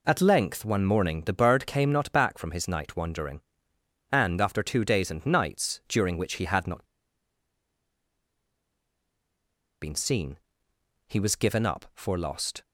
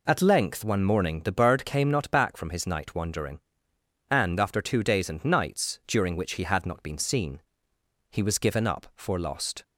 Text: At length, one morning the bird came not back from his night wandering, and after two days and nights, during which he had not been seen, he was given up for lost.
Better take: second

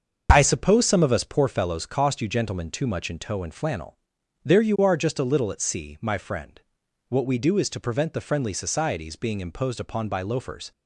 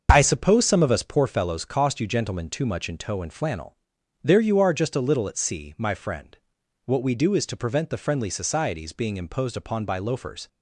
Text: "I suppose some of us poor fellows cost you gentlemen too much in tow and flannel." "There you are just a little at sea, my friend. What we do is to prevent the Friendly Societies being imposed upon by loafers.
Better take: neither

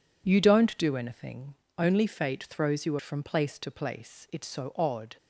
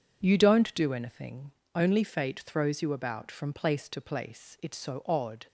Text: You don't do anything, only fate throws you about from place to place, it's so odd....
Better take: second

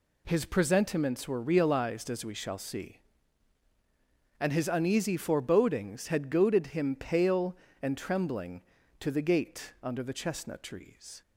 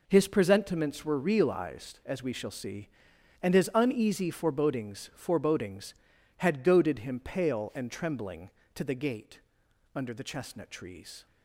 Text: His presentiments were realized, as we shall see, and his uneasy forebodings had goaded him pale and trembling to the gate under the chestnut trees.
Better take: first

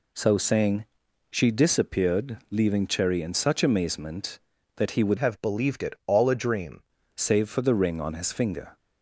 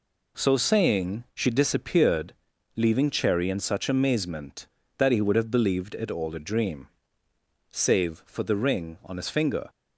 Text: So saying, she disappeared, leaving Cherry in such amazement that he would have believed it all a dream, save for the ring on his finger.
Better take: second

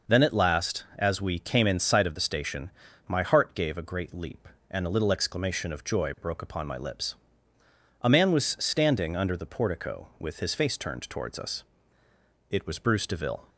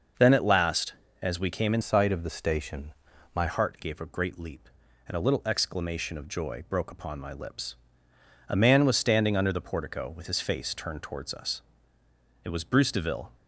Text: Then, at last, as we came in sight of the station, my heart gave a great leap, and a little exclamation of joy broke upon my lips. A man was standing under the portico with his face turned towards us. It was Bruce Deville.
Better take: first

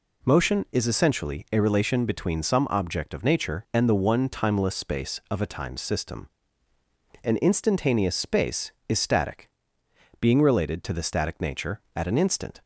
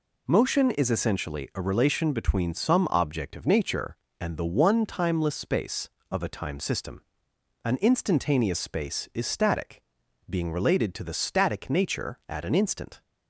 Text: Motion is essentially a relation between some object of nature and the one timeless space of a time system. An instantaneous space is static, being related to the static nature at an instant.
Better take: neither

